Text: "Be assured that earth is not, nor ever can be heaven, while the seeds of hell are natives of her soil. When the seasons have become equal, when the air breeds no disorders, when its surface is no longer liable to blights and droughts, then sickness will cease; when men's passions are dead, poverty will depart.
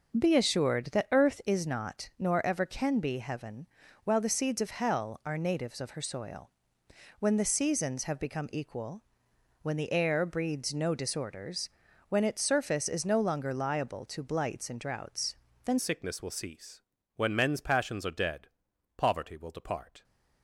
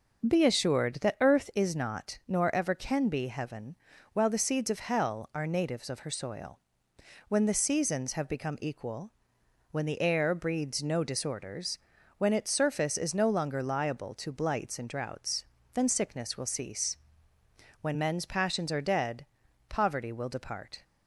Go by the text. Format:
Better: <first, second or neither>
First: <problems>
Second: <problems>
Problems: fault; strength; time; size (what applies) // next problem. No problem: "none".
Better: second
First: changes voice at "sickness"; from 15.7 s on; 4.3 s long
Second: none